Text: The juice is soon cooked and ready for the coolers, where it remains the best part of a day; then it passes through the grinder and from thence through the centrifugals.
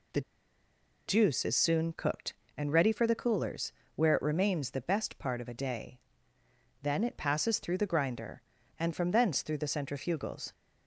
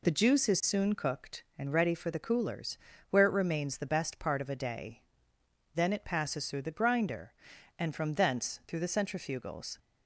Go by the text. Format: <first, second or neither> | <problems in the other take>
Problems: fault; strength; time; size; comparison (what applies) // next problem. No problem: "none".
second | pauses between "The" and "juice"; noticeable; at 0.2 s; 0.86 s long